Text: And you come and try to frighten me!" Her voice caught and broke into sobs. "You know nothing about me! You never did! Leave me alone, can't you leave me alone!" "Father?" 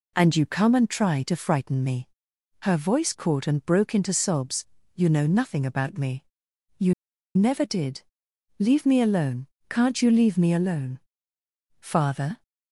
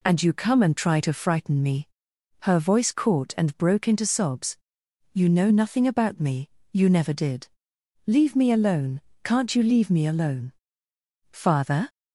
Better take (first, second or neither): second